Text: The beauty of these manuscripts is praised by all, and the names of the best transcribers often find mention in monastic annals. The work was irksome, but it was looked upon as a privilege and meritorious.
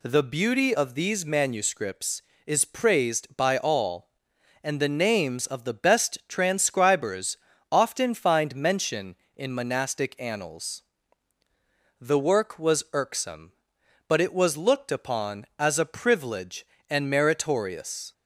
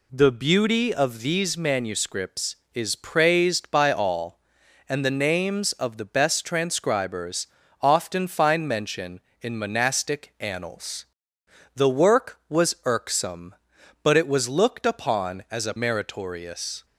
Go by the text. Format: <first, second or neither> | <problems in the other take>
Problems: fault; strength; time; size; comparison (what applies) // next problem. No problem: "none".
first | pauses between "transcribers" and "often"; slight; at 7.4 s; 0.34 s long; slight in the first // skips "privilege and"; at 15.7 s